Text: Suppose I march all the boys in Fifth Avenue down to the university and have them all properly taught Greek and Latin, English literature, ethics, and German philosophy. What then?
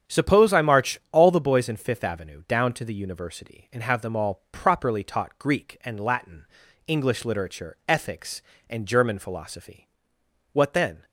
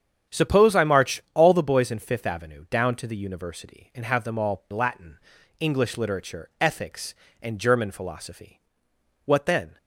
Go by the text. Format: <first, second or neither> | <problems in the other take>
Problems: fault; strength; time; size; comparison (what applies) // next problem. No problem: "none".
first | starts louder than the rest; strong; until 1.4 s; 8 dB; strong in the first // skips "properly taught Greek and"; at 4.6 s